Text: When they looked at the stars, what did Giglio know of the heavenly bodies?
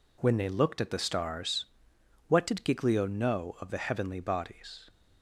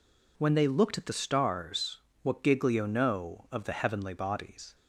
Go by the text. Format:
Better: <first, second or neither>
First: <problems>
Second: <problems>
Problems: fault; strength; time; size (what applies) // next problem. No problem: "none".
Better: first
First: none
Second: skips "did"; at 2.4 s